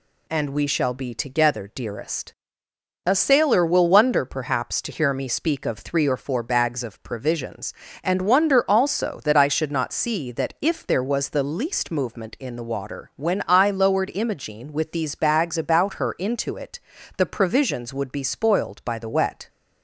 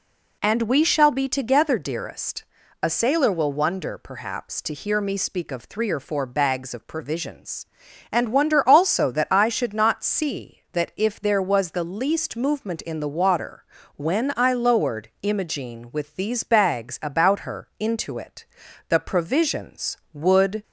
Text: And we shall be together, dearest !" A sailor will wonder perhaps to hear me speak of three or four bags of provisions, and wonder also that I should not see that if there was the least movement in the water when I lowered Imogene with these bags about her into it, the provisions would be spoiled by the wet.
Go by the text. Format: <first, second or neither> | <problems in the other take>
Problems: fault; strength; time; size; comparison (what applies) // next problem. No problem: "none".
first | pauses between "water" and "when"; slight; at 13.6 s; 0.32 s long // stops before "be spoiled by the wet"; at 20.6 s